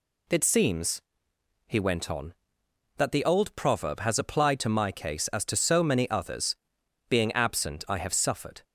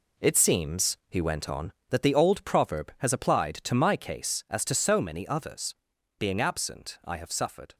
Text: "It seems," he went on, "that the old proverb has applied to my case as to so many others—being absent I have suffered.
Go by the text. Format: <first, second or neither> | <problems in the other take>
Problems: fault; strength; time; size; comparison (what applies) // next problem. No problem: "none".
first | gets quieter; strong; throughout; 8.5 dB